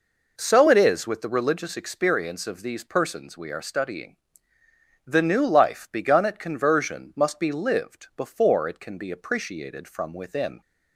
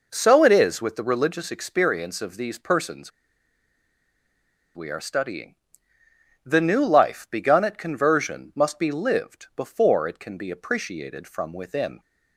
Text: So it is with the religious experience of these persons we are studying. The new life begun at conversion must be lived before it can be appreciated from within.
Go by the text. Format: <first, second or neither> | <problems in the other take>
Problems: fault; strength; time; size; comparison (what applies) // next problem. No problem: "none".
first | pauses between "persons" and "we"; strong; at 3.1 s; 1.6 s long